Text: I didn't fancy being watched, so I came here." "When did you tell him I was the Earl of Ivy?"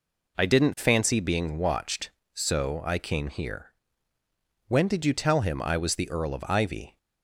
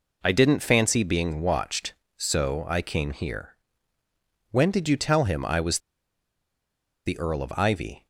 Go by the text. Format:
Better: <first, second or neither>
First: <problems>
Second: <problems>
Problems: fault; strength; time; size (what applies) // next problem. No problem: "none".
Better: first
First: none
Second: pauses between "was" and "the"; strong; at 5.7 s; 1.2 s long